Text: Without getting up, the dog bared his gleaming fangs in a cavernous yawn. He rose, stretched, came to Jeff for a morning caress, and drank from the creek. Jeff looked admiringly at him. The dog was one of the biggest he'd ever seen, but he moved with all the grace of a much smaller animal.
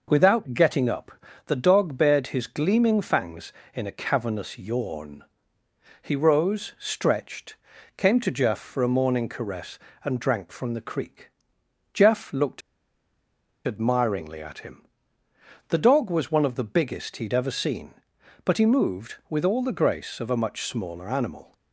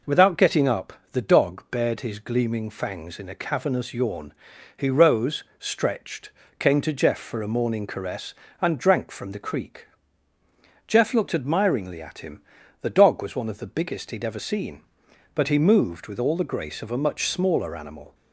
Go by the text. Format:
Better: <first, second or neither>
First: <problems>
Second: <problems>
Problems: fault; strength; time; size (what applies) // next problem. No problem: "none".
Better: second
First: pauses between "looked" and "admiringly"; at 12.6 s; 1.0 s long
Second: none